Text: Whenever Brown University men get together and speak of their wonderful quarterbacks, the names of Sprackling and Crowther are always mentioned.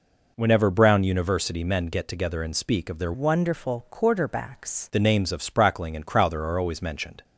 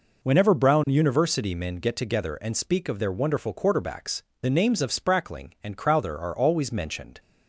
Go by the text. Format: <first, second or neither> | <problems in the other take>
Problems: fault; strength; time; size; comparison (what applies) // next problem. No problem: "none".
second | changes voice from "wonderful" to "quarterbacks"; from 3.1 to 4.9 s; 1.8 s long